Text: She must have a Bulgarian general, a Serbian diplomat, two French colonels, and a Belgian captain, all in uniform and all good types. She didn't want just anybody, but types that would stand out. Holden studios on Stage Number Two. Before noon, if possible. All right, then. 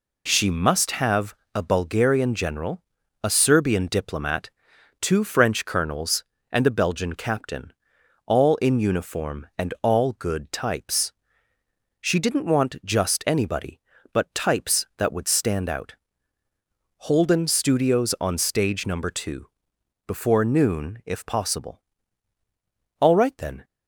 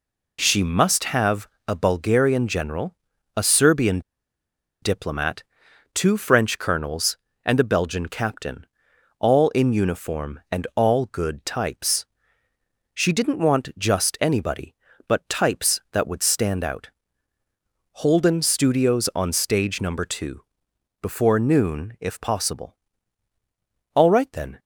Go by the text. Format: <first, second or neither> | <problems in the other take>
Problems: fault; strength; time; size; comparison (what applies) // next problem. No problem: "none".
first | pauses between "have" and "a"; slight; at 1.4 s; 0.18 s long; slight in the first // pauses between "Serbian" and "diplomat"; noticeable; at 3.9 s; 0.82 s long